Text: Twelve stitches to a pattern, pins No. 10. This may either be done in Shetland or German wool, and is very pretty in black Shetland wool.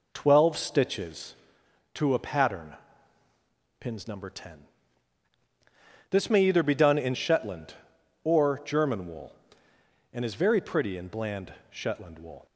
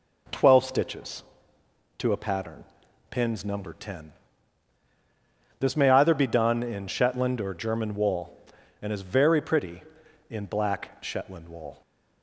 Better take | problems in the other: second | says "bland" for "black"; at 11.0 s

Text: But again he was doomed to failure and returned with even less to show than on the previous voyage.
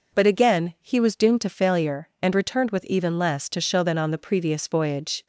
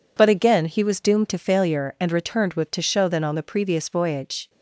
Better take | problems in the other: first | skips "even less"; at 2.7 s

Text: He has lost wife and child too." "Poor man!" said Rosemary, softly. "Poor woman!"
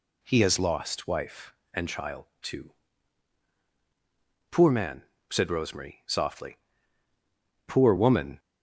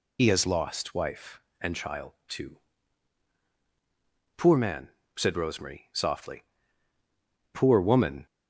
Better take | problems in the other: first | loses the start of "He"; at 0.1 s; 90 ms // pauses between "child" and "too"; slight; at 2.1 s; 0.17 s long; slight in the first

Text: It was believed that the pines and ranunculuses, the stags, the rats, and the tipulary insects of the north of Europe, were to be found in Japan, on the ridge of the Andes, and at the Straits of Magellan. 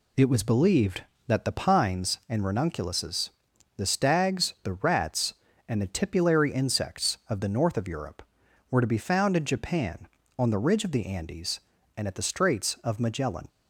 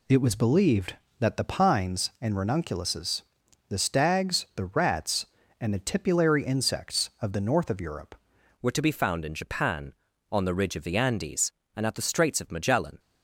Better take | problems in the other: first | changes voice at "were"; from 8.6 s on; 4.3 s long

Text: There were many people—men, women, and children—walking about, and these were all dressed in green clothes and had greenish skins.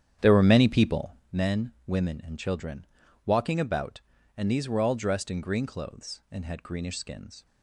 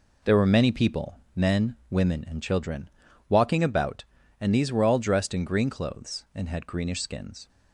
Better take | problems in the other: second | starts louder than the rest; strong; until 1.3 s; 9 dB

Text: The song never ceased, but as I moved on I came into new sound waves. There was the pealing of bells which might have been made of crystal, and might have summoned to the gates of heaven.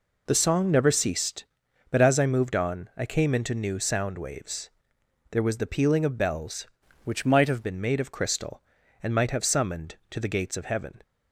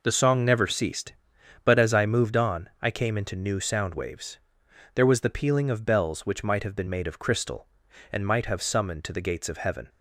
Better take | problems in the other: second | changes voice from "which" to "have"; from 7.0 to 7.6 s; 0.6 s long

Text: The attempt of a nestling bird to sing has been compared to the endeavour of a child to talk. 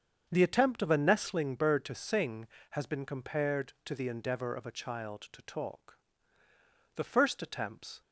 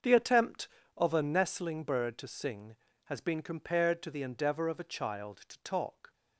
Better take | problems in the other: second | starts louder than the rest; until 1.3 s; 7 dB; also in the second // goes on to say "The first attempts"; noticeable; from 6.9 s on; 1.0 s long

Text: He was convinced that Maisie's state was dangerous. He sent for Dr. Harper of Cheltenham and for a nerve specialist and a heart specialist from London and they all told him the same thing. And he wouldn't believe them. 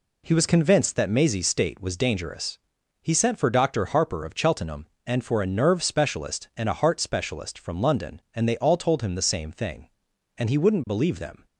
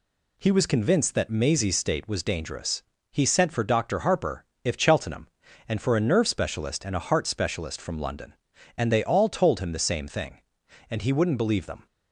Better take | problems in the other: first | says "if" for "of"; at 4.6 s

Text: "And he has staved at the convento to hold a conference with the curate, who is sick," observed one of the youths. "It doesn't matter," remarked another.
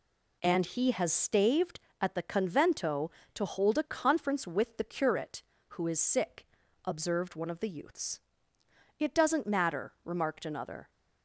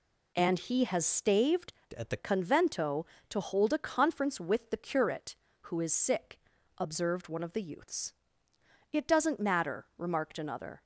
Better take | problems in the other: first | changes voice from "at" to "the"; from 1.9 to 2.1 s; 0.2 s long

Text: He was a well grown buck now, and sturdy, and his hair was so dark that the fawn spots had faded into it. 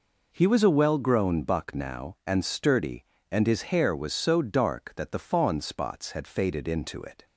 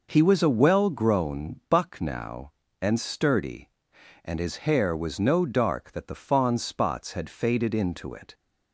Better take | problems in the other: first | says "no" for "so"; at 5.1 s

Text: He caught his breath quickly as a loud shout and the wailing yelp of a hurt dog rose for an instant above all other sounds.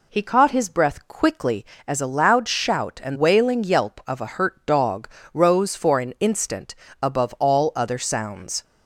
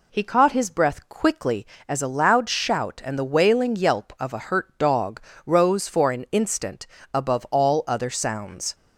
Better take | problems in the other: second | skips "the"; at 3.1 s // pauses between "dog" and "rose"; slight; at 5.0 s; 0.26 s long; slight in the second // pauses between "instant" and "above"; slight; at 6.7 s; 0.30 s long; slight in the second

